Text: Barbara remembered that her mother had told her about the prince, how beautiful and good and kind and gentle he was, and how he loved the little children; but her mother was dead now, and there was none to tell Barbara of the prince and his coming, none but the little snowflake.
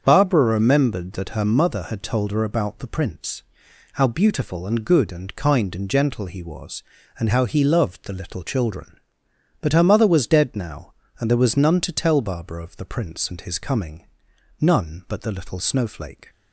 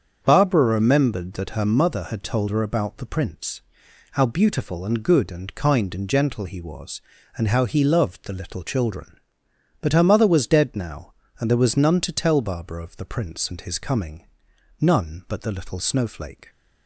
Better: neither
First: starts louder than the rest; strong; until 1.0 s; 7.5 dB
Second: starts louder than the rest; strong; until 1.2 s; 7.5 dB

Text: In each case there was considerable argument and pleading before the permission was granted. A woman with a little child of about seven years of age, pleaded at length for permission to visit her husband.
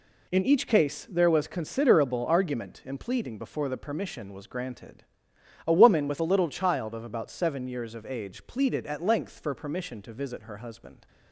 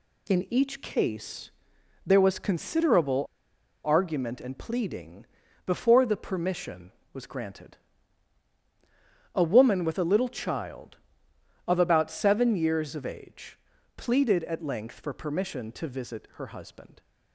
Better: first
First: none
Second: pauses between "case" and "there"; noticeable; at 1.4 s; 0.56 s long // pauses between "considerable" and "argument"; noticeable; at 3.2 s; 0.59 s long // pauses between "pleading" and "before"; at 5.2 s; 0.42 s long

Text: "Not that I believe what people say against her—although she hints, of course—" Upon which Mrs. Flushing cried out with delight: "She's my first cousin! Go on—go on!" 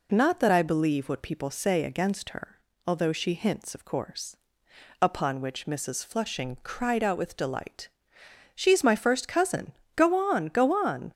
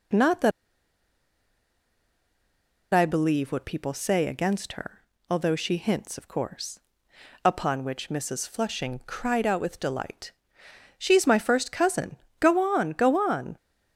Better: first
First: none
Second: pauses between "that" and "I"; strong; at 0.5 s; 2.4 s long

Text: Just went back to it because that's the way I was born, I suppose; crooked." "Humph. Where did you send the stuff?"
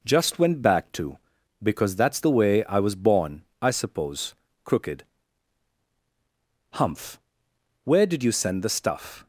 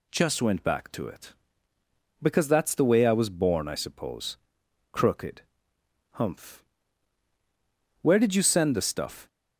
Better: second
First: skips "it"; at 1.4 s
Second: none

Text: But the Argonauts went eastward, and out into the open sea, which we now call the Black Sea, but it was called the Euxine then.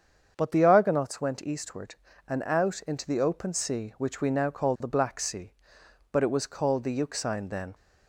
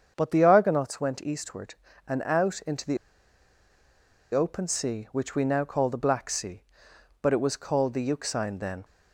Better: first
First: starts louder than the rest; strong; until 1.3 s; 7 dB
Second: starts louder than the rest; strong; until 1.1 s; 7 dB // pauses between "the" and "open"; strong; at 2.9 s; 1.3 s long

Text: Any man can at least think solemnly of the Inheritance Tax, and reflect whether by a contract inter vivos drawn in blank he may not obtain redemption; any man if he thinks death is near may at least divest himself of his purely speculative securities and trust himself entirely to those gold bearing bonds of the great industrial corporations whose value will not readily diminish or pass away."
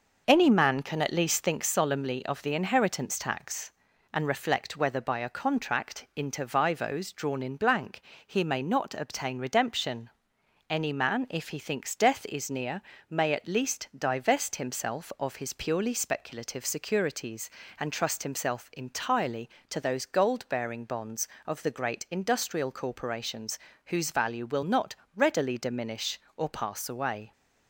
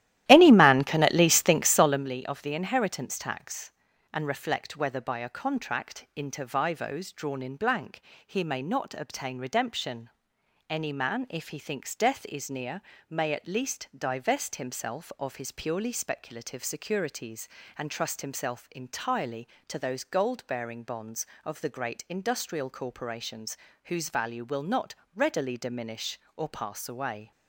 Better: first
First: pauses between "blank" and "he"; slight; at 8.0 s; 0.24 s long // pauses between "near" and "may"; slight; at 12.8 s; 0.30 s long // pauses between "corporations" and "whose"; slight; at 23.5 s; 0.28 s long // pauses between "not" and "readily"; slight; at 24.9 s; 0.22 s long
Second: starts louder than the rest; strong; until 2.0 s; 14 dB // pauses between "blank" and "he"; slight; at 8.0 s; 0.24 s long // pauses between "near" and "may"; slight; at 12.8 s; 0.30 s long // pauses between "corporations" and "whose"; slight; at 23.5 s; 0.28 s long // pauses between "not" and "readily"; slight; at 24.9 s; 0.22 s long

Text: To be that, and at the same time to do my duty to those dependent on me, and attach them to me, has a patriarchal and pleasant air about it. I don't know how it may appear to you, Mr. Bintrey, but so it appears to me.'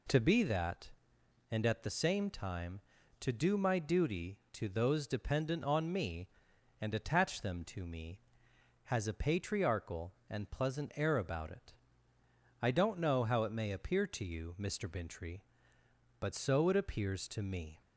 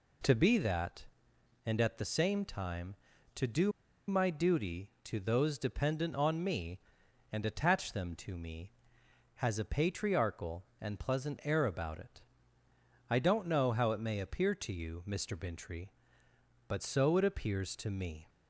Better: first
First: none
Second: pauses between "do" and "my"; at 3.7 s; 0.37 s long

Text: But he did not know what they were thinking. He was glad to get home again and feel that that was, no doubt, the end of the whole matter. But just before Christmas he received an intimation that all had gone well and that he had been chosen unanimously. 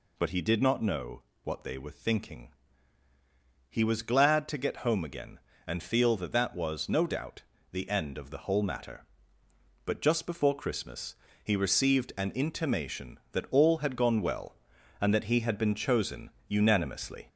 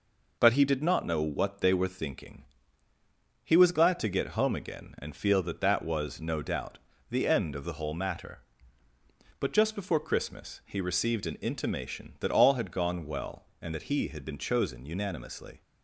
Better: second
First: gets louder; slight; throughout; 3 dB // pauses between "know" and "what"; slight; at 1.2 s; 0.22 s long // pauses between "Christmas" and "he"; slight; at 11.1 s; 0.30 s long // pauses between "chosen" and "unanimously"; slight; at 16.2 s; 0.18 s long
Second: none

